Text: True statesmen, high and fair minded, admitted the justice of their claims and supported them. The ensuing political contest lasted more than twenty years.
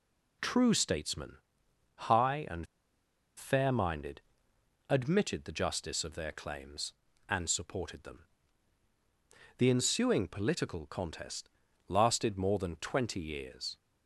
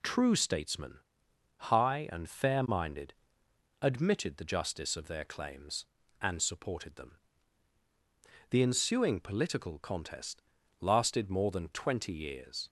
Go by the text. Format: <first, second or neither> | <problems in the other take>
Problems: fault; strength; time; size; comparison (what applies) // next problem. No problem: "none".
second | pauses between "and" and "fair"; noticeable; at 2.6 s; 0.71 s long // pauses between "contest" and "lasted"; at 11.4 s; 0.40 s long; also in the second